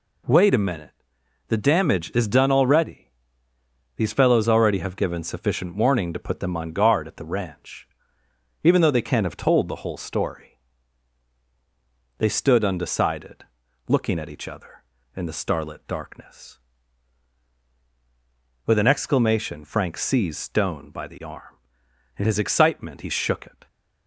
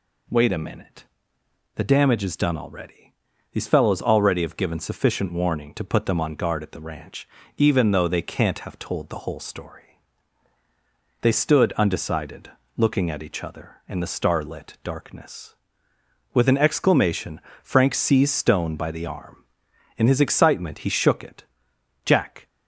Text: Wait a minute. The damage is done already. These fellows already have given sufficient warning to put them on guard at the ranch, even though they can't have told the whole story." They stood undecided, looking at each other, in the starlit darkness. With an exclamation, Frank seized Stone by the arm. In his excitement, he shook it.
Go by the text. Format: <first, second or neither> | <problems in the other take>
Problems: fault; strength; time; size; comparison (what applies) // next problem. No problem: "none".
first | goes on to say "Jack"; slight; from 22.0 s on; 0.42 s long